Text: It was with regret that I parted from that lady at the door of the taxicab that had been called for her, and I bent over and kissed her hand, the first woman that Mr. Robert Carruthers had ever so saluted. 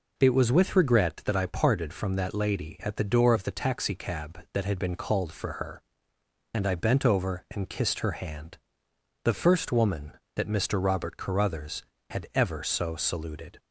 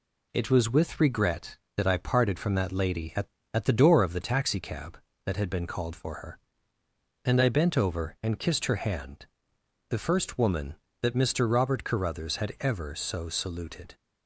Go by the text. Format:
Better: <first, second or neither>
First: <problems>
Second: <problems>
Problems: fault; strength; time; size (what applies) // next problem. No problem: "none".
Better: first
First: none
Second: says "at" twice; at 3.5 s